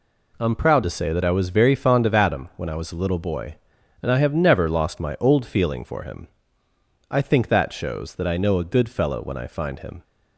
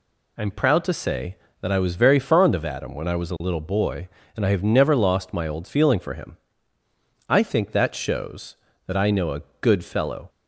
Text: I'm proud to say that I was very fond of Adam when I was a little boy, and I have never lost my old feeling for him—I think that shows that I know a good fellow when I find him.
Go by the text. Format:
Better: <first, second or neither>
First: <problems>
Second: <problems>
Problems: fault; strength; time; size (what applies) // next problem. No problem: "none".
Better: first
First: none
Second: pauses between "a" and "good"; slight; at 9.4 s; 0.20 s long // stops before "when I find him"; at 10.2 s